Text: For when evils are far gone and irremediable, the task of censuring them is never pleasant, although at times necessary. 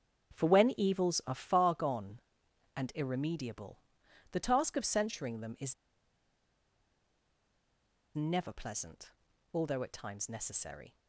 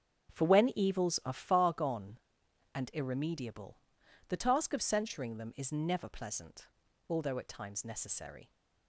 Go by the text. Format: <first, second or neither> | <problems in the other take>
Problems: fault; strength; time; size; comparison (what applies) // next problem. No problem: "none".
second | starts louder than the rest; strong; until 1.4 s; 7 dB; strong in the second // pauses between "is" and "never"; strong; at 5.7 s; 2.4 s long